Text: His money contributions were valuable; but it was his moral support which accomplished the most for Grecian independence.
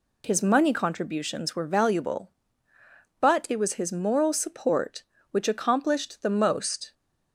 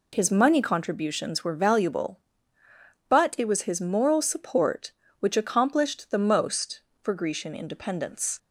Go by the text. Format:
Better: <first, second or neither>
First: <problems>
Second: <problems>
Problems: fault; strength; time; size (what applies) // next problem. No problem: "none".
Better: second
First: stops before "for Grecian independence"; at 6.9 s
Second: none